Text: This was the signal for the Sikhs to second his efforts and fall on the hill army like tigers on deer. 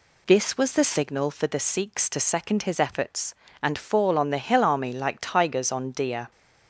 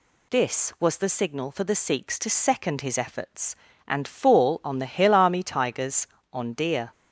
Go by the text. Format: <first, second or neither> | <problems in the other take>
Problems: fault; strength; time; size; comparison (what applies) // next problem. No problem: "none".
first | skips "like"; at 5.4 s